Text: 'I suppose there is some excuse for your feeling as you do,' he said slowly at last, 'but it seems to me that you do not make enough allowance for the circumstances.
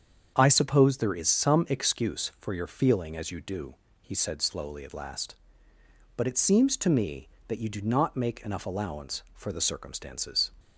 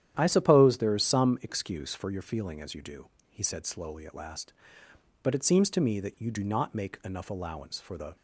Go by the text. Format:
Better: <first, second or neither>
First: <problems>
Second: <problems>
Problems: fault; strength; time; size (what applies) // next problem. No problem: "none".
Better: first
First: starts louder than the rest; strong; until 1.3 s; 7.5 dB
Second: starts louder than the rest; strong; until 1.2 s; 10.5 dB // stops before "circumstances"; at 8.1 s